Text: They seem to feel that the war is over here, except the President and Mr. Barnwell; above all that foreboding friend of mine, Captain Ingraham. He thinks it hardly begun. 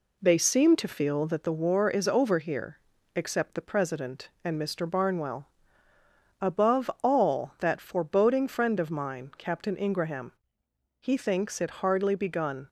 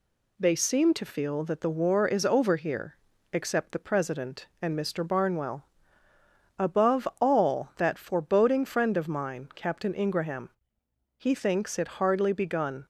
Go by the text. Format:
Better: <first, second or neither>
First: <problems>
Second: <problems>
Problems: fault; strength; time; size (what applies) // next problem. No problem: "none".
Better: second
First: starts louder than the rest; slight; until 1.5 s; 3 dB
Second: none